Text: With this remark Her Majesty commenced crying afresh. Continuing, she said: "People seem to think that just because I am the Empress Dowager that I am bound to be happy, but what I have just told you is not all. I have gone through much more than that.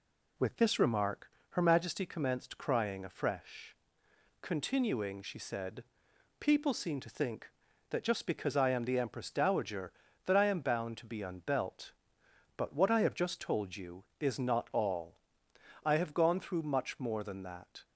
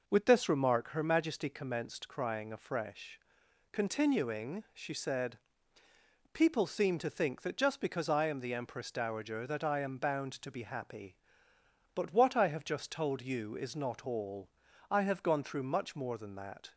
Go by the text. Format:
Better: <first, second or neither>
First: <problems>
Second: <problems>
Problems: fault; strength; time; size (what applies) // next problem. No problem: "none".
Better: second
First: pauses between "remark" and "Her"; slight; at 1.3 s; 0.20 s long // says "unbelt" for "happy"; at 11.2 s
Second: none